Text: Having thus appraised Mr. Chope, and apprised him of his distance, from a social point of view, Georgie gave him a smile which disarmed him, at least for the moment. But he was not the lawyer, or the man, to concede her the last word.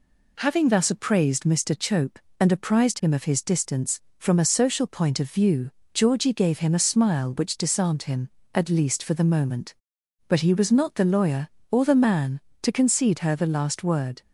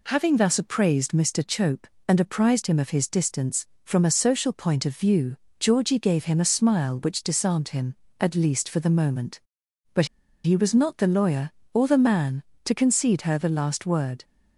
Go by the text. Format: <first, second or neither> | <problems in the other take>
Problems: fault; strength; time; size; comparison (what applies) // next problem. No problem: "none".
first | pauses between "But" and "he"; at 10.0 s; 0.37 s long